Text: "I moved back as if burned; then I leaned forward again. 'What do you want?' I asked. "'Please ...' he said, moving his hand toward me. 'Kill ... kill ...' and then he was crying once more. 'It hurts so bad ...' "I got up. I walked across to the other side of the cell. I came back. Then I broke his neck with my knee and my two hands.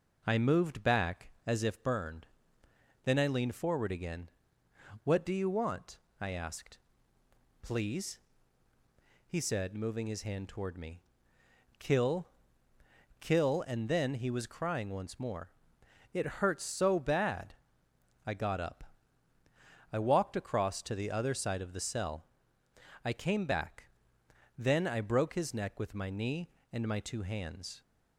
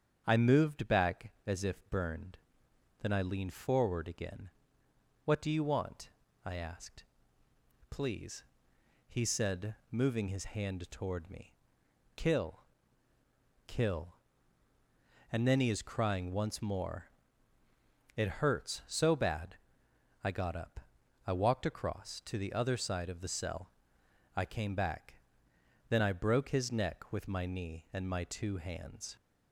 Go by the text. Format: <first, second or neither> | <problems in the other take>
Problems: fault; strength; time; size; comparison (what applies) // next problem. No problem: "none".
first | starts louder than the rest; strong; until 1.2 s; 8.5 dB; noticeable in the first // says "is" for "was"; at 15.7 s